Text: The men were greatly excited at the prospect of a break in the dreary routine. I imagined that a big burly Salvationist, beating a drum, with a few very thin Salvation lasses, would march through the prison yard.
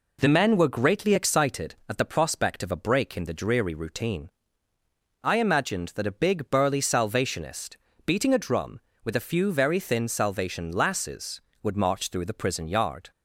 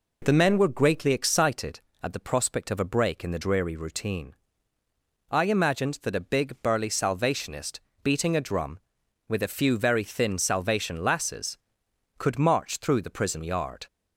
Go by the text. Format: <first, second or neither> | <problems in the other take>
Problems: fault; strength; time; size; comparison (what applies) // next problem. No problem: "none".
first | says "could" for "would"; at 12.1 s